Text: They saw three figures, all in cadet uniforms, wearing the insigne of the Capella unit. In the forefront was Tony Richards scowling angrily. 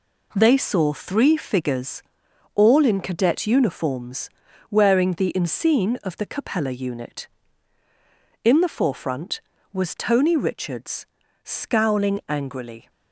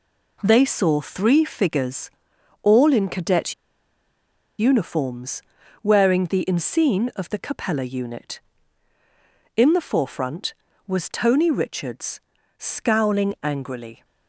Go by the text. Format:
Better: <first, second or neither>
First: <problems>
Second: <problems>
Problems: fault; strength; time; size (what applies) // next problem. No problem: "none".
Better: first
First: pauses between "Richards" and "scowling"; slight; at 11.0 s; 0.36 s long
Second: pauses between "cadet" and "uniforms"; at 3.5 s; 1.0 s long // pauses between "Richards" and "scowling"; slight; at 12.2 s; 0.36 s long